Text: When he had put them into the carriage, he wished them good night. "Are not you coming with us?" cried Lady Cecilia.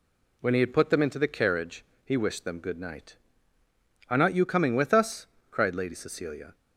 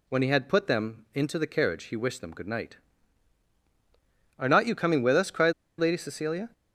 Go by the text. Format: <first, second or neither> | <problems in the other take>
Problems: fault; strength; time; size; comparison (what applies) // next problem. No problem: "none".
first | pauses between "cried" and "Lady"; slight; at 5.5 s; 0.26 s long